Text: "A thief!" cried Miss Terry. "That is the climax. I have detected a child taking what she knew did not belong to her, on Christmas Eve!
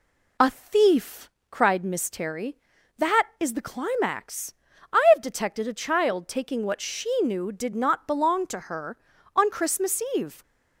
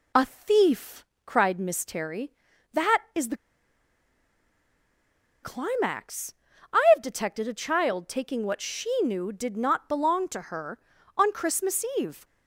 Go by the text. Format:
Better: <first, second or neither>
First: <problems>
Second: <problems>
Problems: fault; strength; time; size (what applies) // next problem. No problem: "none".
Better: first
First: none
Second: pauses between "the" and "climax"; strong; at 3.3 s; 2.0 s long